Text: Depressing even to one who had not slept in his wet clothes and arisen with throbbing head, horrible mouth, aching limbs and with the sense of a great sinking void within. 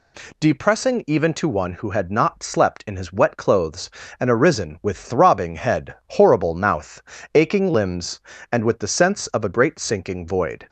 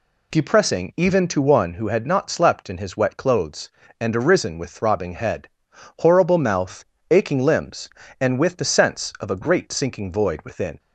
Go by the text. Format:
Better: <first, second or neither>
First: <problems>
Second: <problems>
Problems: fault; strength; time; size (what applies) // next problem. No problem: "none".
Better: second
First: stops before "within"; at 10.6 s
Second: none